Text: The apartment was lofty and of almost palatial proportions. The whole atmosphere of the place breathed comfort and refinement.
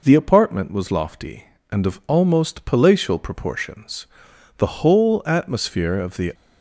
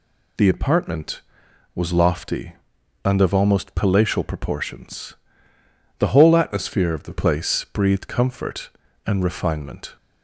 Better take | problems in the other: second | stops before "place breathed comfort and refinement"; at 6.3 s

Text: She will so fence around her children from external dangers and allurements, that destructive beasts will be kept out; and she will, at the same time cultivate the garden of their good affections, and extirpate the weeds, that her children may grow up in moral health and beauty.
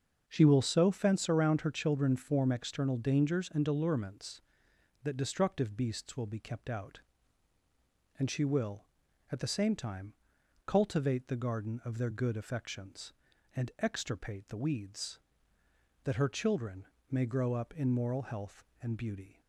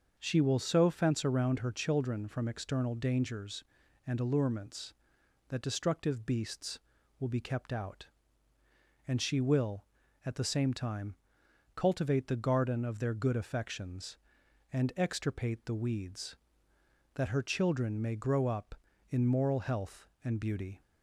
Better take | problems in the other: second | starts louder than the rest; until 1.2 s; 6.5 dB; also in the second // says "form" for "from"; at 2.1 s // pauses between "time" and "cultivate"; noticeable; at 10.1 s; 0.52 s long; noticeable in the second // pauses between "children" and "may"; slight; at 16.8 s; 0.24 s long

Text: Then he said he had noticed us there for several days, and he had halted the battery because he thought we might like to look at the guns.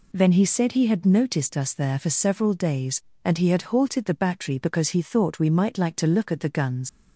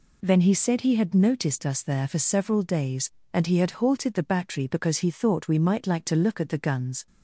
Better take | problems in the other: second | leaves "guns" unfinished; at 6.8 s; 85 ms

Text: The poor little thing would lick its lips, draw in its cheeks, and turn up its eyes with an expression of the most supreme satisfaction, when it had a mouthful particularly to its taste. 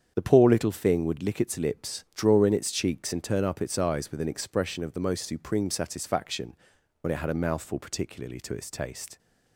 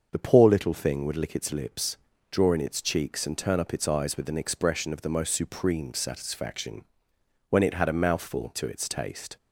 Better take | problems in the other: first | starts louder than the rest; until 1.1 s; 6.5 dB; strong in the first // skips "particularly"; at 8.5 s

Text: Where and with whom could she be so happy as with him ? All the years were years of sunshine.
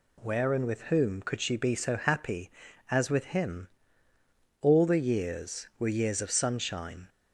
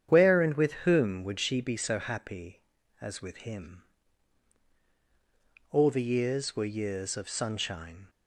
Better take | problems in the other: first | starts louder than the rest; strong; until 1.1 s; 9 dB // says "would" for "could"; at 1.2 s

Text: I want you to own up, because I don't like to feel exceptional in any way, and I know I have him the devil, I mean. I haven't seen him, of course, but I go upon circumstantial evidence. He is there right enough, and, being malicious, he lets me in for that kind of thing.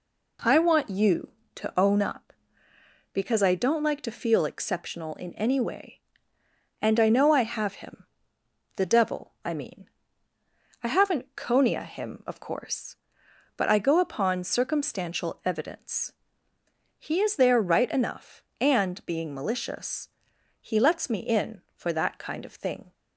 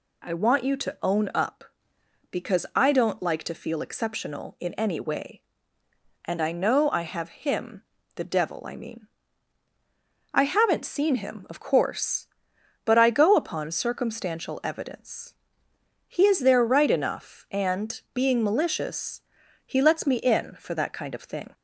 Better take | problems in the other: second | pauses between "him" and "the"; noticeable; at 8.0 s; 0.72 s long; slight in the second // says "conia" for "seen"; at 11.3 s

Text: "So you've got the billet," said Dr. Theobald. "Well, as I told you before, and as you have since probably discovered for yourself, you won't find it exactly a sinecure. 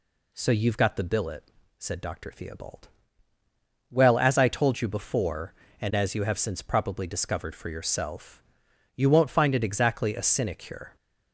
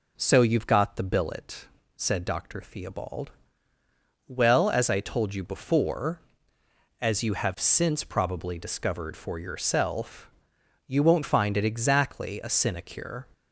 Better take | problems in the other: first | skips "and"; at 6.6 s

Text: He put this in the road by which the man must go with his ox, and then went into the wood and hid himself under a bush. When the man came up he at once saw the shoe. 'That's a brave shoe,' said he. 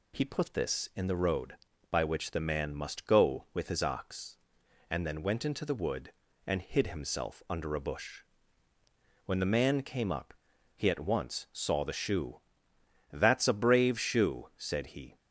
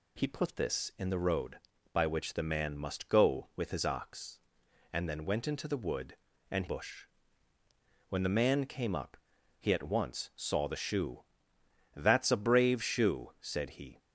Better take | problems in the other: first | skips "hid himself under a"; at 6.6 s // pauses between "up" and "he"; at 9.1 s; 0.40 s long; also in the first

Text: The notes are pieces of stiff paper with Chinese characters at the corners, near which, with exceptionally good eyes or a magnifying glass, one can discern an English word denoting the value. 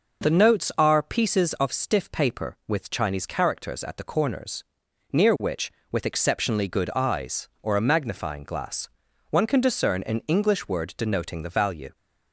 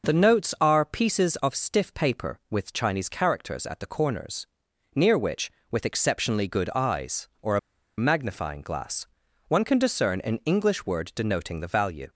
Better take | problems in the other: first | pauses between "a" and "magnifying"; at 7.5 s; 0.39 s long

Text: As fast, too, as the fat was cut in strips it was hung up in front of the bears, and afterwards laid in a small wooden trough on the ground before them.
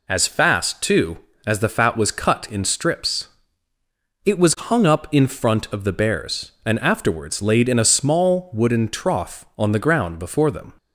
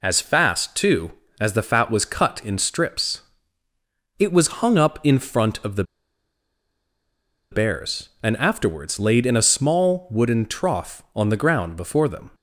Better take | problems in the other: first | pauses between "strips" and "it"; noticeable; at 3.2 s; 0.96 s long; noticeable in the first // pauses between "the" and "bears"; strong; at 5.8 s; 1.6 s long

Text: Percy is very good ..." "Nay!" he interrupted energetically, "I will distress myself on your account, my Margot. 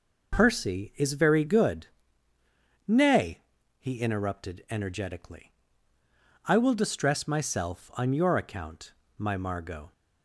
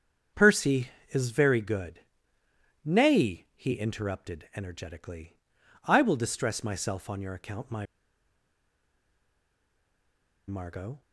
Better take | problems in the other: first | starts louder than the rest; strong; until 1.5 s; 8 dB // pauses between "my" and "Margot"; strong; at 7.8 s; 2.6 s long

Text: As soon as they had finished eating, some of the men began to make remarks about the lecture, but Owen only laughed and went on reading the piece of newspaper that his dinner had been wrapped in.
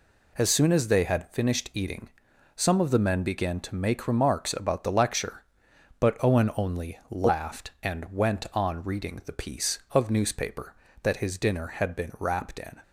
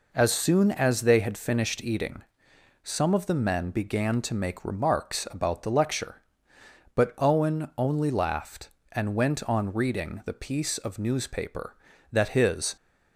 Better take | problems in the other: first | stops before "dinner had been wrapped in"; at 12.7 s

